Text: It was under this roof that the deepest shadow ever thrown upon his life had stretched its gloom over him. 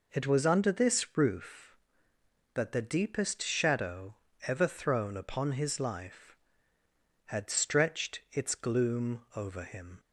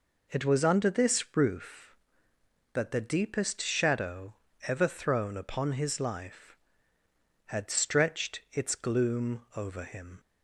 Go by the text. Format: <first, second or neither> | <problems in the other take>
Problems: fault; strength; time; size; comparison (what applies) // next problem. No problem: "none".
neither | pauses between "shadow" and "ever"; slight; the same in both